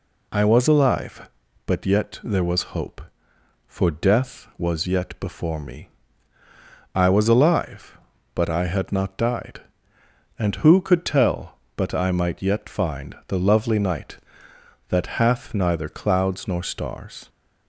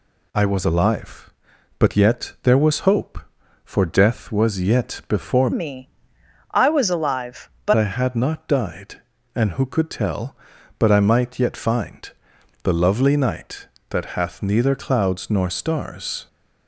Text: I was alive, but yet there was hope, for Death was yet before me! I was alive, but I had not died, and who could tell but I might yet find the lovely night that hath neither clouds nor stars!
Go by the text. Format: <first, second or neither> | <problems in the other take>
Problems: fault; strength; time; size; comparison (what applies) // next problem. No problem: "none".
first | changes voice from "me" to "but"; from 5.5 to 7.7 s; 2.2 s long // pauses between "find" and "the"; noticeable; at 12.0 s; 0.54 s long